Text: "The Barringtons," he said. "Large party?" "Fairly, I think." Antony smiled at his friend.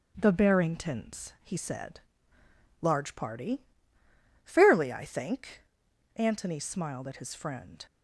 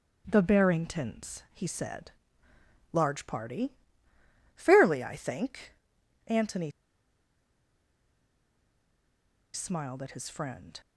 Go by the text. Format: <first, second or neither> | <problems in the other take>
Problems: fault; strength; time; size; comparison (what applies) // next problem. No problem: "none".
first | starts louder than the rest; strong; until 1.2 s; 8 dB; strong in the first // pauses between "Antony" and "smiled"; strong; at 6.7 s; 2.8 s long